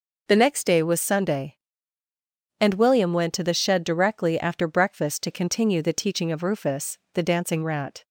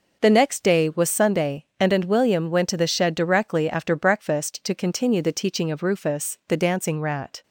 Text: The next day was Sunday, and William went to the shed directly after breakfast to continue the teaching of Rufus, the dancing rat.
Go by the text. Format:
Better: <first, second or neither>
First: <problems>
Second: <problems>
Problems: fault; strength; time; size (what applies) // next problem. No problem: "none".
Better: first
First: none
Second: says "and" twice; at 1.9 s